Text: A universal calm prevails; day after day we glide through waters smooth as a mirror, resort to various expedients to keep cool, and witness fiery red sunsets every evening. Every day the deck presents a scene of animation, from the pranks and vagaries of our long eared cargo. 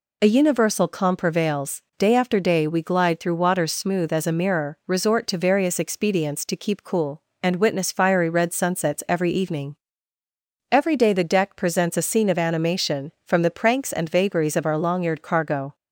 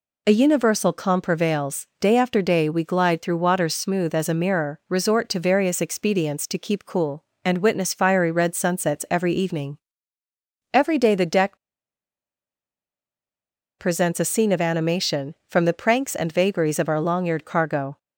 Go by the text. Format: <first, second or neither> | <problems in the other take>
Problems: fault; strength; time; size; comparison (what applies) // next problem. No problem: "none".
first | pauses between "deck" and "presents"; strong; at 11.5 s; 2.2 s long